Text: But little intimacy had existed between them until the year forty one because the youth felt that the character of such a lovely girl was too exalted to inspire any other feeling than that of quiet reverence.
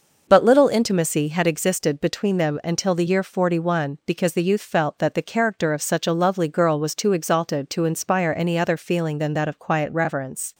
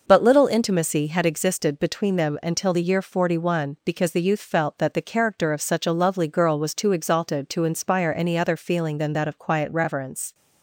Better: neither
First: none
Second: none

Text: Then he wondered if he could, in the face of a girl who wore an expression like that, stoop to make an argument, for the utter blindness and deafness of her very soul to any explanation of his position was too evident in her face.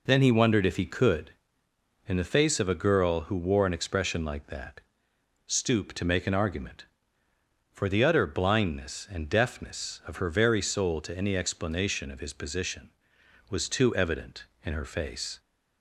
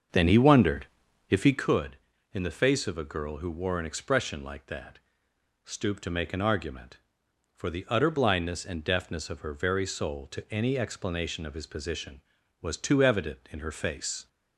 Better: first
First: none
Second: starts louder than the rest; until 1.7 s; 6.5 dB // pauses between "wondered" and "if"; at 0.8 s; 0.44 s long

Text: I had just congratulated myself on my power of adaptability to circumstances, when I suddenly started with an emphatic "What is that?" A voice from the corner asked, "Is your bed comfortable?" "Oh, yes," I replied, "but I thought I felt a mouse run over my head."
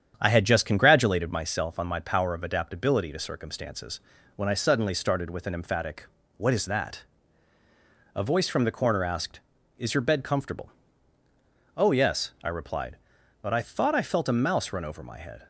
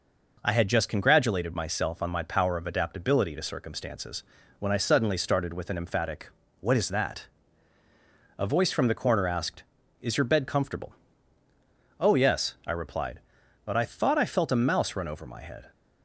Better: second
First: starts louder than the rest; strong; until 1.5 s; 8.5 dB // pauses between "emphatic" and "What"; slight; at 6.0 s; 0.30 s long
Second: pauses between "emphatic" and "What"; slight; at 6.3 s; 0.30 s long

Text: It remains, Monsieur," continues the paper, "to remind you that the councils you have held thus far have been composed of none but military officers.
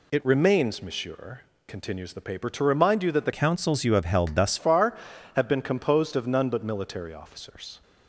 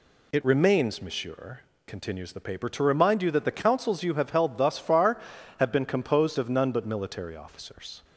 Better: second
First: changes voice from "councils" to "thus"; from 3.3 to 4.5 s; 1.2 s long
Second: none

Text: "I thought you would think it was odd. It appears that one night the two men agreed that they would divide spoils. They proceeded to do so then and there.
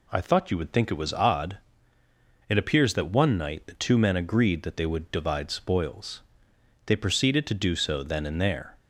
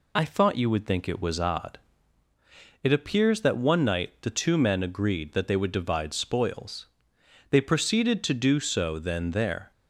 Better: first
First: none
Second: skips "and"; at 9.3 s

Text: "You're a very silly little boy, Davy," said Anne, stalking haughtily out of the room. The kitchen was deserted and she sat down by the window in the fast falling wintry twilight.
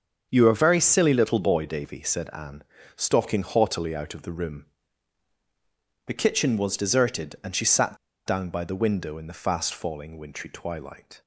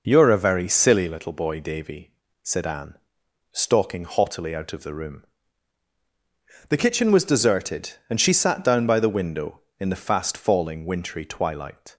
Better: second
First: starts louder than the rest; until 1.3 s; 7 dB // pauses between "sat" and "down"; slight; at 7.9 s; 0.29 s long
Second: none

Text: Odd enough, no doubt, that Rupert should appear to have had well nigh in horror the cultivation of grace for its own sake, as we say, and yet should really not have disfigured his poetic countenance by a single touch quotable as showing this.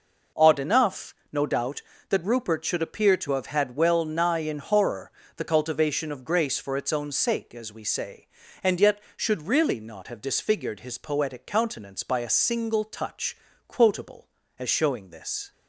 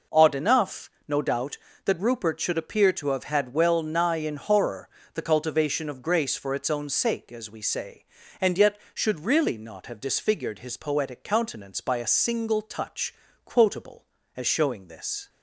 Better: neither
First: pauses between "horror" and "the"; slight; at 5.1 s; 0.24 s long // pauses between "touch" and "quotable"; slight; at 13.3 s; 0.32 s long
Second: pauses between "horror" and "the"; slight; at 4.8 s; 0.24 s long // pauses between "touch" and "quotable"; slight; at 13.1 s; 0.32 s long

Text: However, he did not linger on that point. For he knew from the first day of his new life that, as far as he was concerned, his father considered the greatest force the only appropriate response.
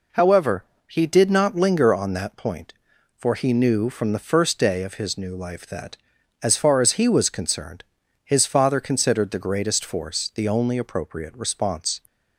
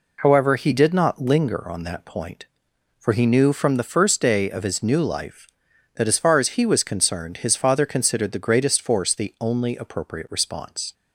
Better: neither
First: none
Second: none

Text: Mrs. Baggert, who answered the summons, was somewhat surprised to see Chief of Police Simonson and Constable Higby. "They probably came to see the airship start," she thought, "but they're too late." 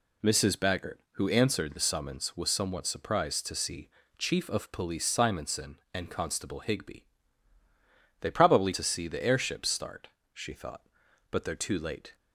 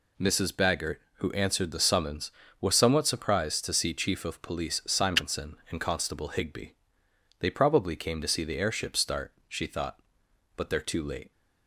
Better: second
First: pauses between "see" and "Chief"; slight; at 3.8 s; 0.28 s long // skips "came"; at 8.7 s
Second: none

